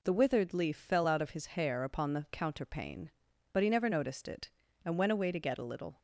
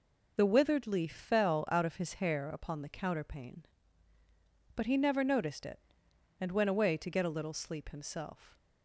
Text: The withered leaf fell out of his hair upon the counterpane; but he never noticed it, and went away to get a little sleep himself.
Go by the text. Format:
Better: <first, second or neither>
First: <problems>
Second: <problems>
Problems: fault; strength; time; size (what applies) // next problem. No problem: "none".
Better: second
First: stops before "sleep himself"; at 5.9 s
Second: none